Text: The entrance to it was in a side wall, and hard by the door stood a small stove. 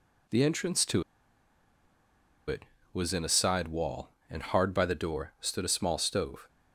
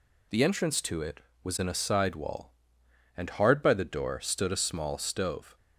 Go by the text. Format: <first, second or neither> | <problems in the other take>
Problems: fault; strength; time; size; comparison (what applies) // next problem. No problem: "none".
second | pauses between "to" and "it"; strong; at 1.0 s; 1.4 s long